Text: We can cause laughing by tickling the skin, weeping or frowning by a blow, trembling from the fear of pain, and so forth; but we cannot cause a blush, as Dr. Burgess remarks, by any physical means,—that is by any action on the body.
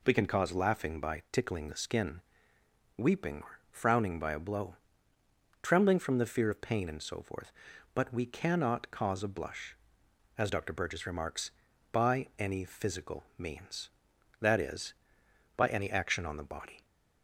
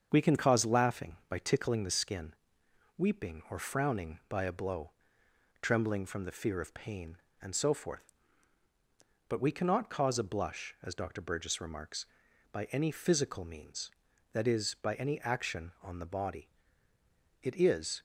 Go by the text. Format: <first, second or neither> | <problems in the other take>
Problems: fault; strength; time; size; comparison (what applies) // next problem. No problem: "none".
first | starts louder than the rest; until 1.1 s; 7 dB // goes on to say "It is"; from 17.4 s on; 0.60 s long